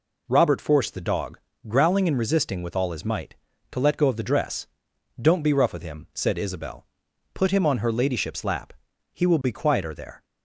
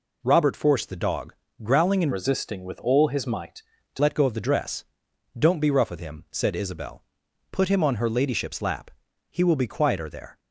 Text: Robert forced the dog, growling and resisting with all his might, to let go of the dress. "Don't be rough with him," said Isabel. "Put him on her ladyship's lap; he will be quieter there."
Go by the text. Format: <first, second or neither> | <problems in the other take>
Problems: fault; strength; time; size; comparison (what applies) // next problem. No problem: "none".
first | changes voice from "resisting" to "to"; from 2.1 to 3.9 s; 1.8 s long